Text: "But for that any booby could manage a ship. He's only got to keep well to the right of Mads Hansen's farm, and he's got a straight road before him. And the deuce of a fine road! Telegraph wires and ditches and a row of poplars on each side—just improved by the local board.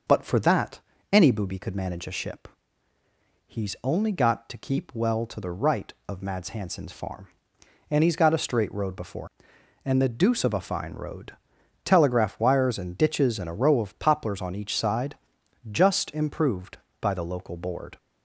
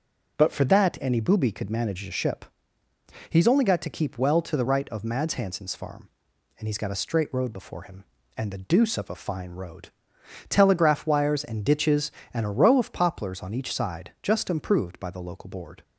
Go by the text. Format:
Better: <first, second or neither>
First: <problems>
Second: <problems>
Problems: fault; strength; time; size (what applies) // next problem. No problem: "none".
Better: second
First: pauses between "that" and "any"; slight; at 0.8 s; 0.32 s long // skips "him"; at 9.5 s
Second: none